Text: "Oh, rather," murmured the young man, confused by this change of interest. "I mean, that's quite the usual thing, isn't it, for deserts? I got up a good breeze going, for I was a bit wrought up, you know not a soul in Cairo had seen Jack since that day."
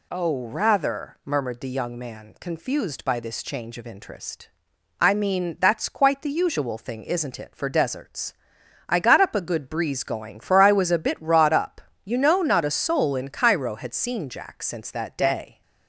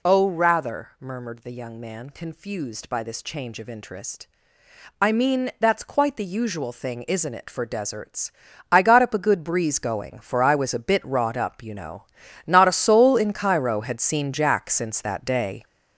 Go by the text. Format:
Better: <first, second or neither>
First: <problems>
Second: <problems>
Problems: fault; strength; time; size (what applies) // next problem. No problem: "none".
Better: first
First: none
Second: gets louder; strong; throughout; 7.5 dB // pauses between "know" and "not"; at 12.0 s; 0.42 s long